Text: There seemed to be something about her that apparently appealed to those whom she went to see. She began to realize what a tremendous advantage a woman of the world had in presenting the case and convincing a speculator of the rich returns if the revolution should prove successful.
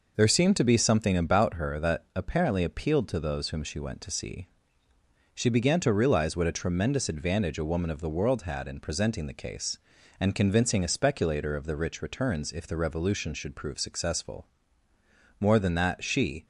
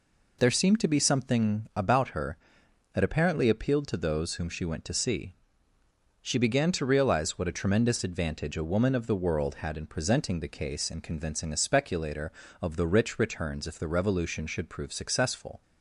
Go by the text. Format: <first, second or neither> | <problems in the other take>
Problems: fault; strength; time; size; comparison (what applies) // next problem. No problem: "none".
second | goes on to say "More than that she"; noticeable; from 15.4 s on; 1.0 s long